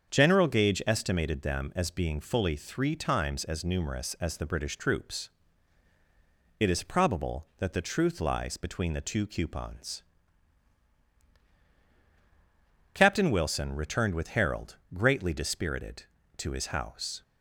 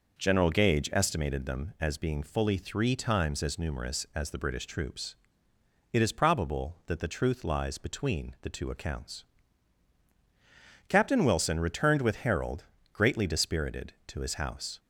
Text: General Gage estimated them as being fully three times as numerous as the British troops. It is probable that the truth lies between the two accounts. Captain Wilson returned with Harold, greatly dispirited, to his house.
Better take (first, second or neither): second